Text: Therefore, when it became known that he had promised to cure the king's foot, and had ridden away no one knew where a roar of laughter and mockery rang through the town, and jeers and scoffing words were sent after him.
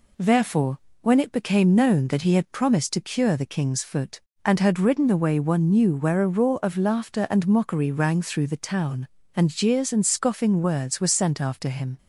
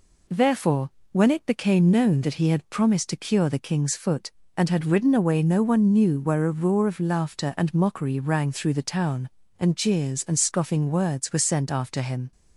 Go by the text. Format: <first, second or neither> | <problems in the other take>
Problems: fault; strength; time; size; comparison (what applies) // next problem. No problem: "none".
second | skips "no"; at 5.3 s